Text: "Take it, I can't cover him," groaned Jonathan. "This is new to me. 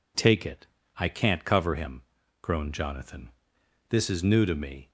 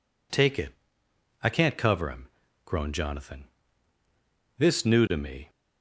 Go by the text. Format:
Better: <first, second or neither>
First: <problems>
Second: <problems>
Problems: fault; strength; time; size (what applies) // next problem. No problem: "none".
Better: first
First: none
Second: skips "is"; at 4.8 s